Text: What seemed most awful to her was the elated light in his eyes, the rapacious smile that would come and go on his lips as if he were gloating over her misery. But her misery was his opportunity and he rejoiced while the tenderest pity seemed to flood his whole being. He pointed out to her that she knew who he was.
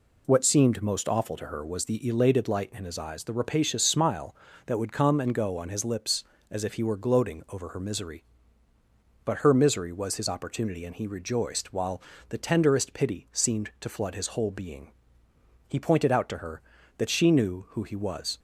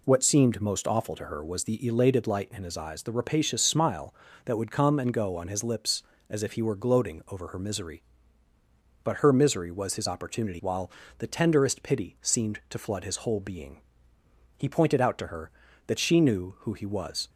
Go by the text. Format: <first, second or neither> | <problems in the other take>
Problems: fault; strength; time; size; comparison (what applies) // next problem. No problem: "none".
first | skips "and he rejoiced"; at 10.6 s // pauses between "while" and "the"; slight; at 10.9 s; 0.28 s long; slight in the first